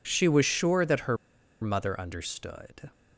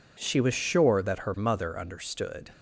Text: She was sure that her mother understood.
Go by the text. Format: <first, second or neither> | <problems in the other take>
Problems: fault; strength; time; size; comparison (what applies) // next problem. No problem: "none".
second | pauses between "her" and "mother"; noticeable; at 1.1 s; 0.46 s long